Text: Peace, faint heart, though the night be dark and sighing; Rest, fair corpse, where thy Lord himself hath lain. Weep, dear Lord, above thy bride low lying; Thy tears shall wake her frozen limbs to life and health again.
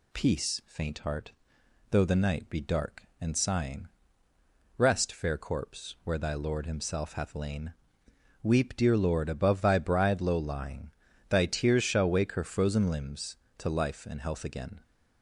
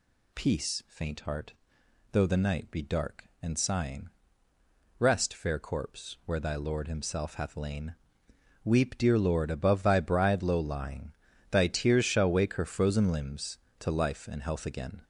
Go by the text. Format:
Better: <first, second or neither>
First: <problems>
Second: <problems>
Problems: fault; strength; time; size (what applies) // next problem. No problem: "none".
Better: first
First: none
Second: gets louder; noticeable; throughout; 5 dB